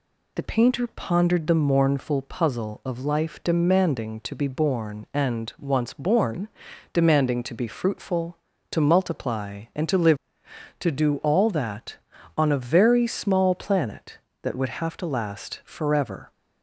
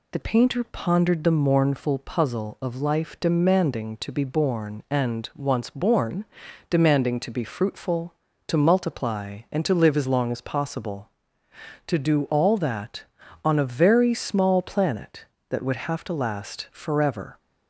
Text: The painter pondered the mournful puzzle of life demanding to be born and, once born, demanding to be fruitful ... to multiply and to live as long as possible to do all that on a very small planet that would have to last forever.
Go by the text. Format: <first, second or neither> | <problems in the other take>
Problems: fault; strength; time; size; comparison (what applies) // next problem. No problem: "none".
second | skips "as long as possible"; at 10.4 s